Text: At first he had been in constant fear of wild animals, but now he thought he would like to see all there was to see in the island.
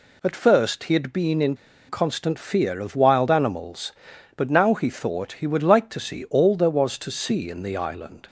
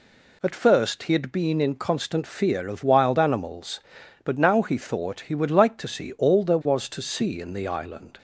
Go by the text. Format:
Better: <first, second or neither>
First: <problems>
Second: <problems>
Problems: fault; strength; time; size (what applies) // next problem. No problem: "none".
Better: second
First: pauses between "in" and "constant"; slight; at 1.5 s; 0.33 s long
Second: none